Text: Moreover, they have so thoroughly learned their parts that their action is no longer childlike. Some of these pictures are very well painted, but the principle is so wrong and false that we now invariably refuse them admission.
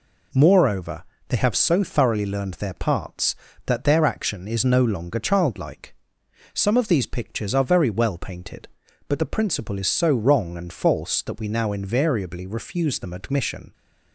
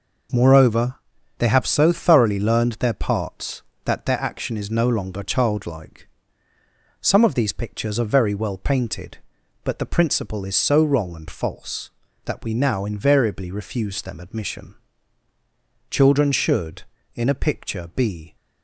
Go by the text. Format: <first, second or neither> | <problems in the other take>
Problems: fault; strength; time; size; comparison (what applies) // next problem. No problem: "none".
first | goes on to say "Children should in a picture be"; strong; from 15.8 s on; 2.4 s long